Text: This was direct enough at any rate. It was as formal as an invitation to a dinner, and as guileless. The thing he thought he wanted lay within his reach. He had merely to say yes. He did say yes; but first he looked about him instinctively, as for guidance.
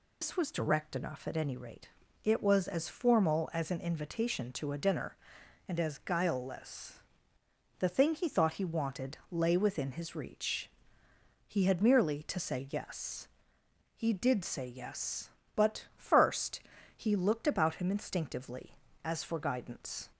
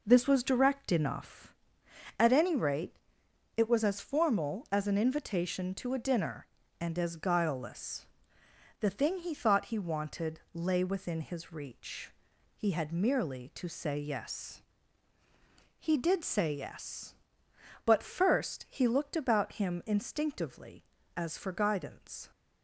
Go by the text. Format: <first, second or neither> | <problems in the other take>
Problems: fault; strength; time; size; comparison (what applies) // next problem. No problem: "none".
second | loses the start of "This"; at 0.2 s; 150 ms // pauses between "first" and "he"; slight; at 16.6 s; 0.36 s long